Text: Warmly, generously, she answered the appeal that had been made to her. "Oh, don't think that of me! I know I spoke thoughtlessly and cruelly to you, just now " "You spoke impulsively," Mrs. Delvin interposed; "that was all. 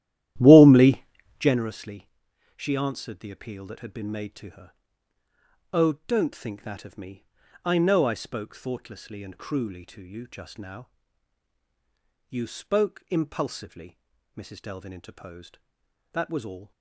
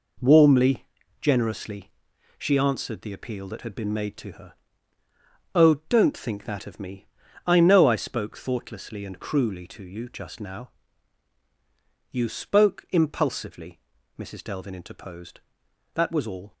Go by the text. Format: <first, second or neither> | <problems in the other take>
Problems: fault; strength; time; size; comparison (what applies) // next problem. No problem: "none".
second | starts louder than the rest; strong; until 1.6 s; 13 dB